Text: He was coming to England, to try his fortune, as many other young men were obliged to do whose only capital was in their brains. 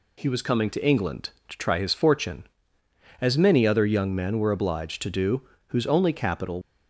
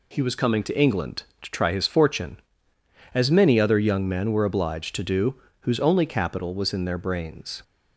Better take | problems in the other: second | pauses between "do" and "whose"; slight; at 5.4 s; 0.24 s long; slight in the second // stops before "was in their brains"; at 6.6 s

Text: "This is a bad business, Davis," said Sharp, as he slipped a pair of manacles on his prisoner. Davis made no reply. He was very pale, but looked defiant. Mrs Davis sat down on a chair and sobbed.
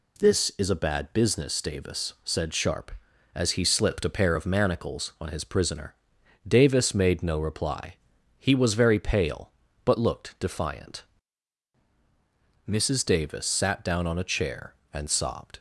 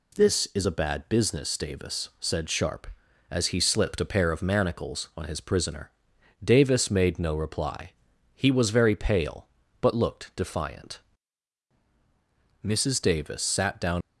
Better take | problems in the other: first | stops before "on a chair and sobbed"; at 14.0 s

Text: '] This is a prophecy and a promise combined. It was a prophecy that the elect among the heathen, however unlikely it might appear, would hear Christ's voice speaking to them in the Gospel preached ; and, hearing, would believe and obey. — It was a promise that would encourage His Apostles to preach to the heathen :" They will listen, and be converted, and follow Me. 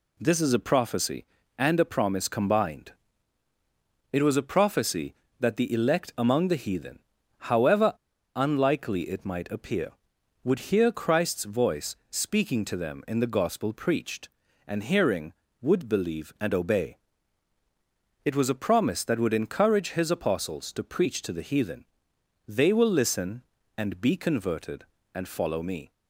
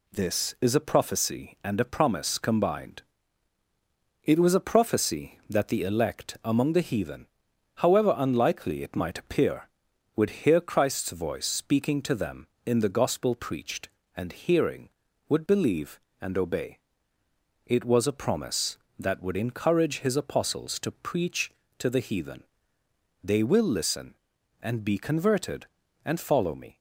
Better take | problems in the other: second | pauses between "however" and "unlikely"; at 7.9 s; 0.41 s long

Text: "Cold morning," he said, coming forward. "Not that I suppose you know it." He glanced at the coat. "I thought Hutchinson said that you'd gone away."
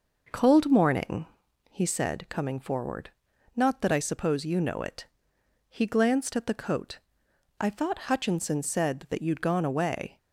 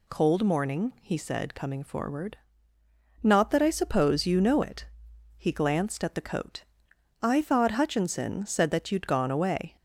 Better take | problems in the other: second | starts louder than the rest; noticeable; until 1.4 s; 5.5 dB

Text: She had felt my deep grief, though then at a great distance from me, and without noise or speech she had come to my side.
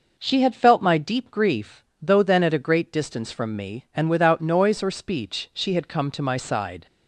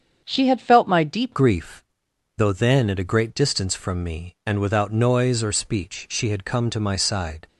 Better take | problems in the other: first | starts louder than the rest; strong; until 1.2 s; 7.5 dB // changes voice at "grief"; from 1.3 s on; 6.1 s long

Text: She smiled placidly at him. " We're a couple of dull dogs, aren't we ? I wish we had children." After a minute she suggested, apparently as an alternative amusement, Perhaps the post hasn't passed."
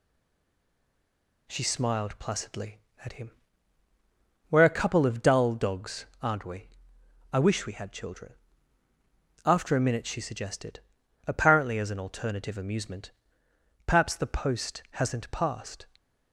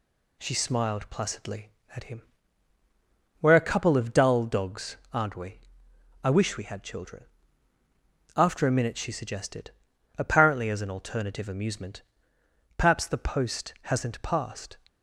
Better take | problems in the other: second | stays silent before the first word; noticeable; until 1.4 s; 1.4 s long

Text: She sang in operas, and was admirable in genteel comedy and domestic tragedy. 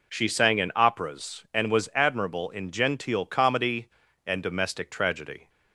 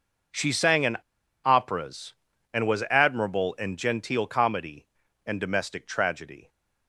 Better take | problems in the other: first | pauses between "in" and "operas"; noticeable; at 0.9 s; 0.49 s long

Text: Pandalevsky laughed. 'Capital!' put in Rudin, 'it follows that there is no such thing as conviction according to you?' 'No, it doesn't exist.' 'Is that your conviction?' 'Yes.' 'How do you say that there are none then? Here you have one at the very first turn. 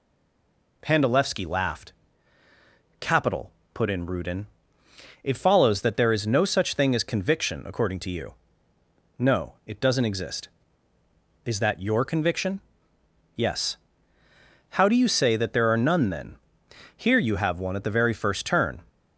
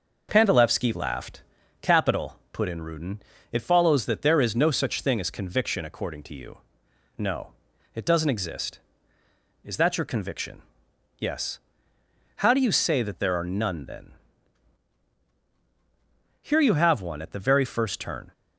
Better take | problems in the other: second | stays silent before the first word; slight; until 0.8 s; 0.8 s long

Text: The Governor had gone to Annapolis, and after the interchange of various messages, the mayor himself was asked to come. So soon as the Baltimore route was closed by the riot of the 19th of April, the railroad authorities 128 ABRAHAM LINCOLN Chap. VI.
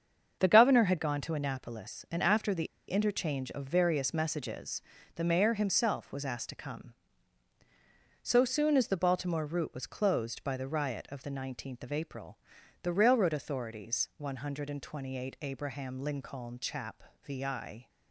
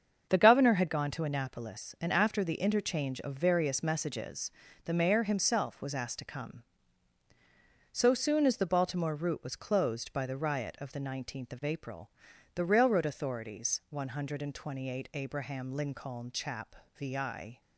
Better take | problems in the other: second | starts louder than the rest; until 1.4 s; 7 dB; also in the second // pauses between "the" and "interchange"; slight; at 2.6 s; 0.22 s long

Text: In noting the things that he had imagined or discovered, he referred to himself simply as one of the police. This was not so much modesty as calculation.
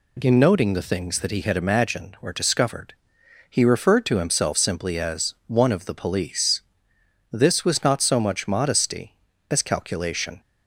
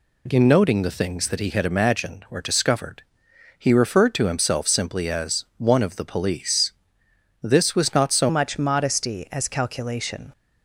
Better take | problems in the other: first | changes voice at "much"; from 8.2 s on; 2.1 s long

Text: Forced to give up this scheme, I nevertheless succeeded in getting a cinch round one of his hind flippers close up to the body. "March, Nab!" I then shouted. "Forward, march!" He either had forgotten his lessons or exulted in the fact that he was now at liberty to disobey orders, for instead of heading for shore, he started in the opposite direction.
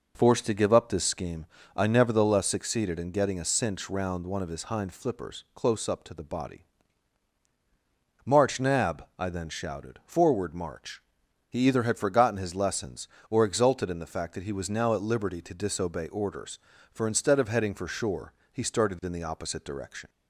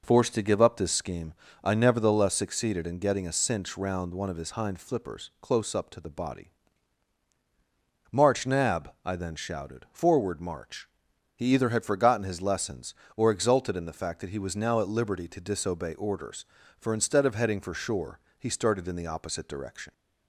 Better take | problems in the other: neither | none

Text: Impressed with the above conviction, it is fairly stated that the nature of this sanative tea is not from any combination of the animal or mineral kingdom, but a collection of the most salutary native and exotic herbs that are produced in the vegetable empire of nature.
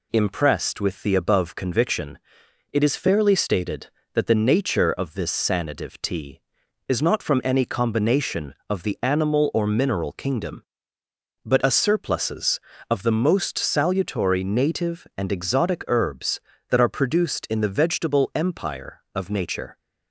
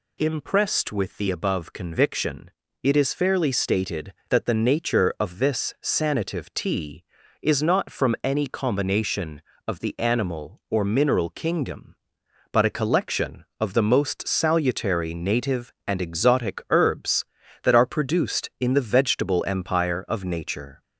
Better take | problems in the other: second | says "surpluses" for "collection"; at 11.7 s

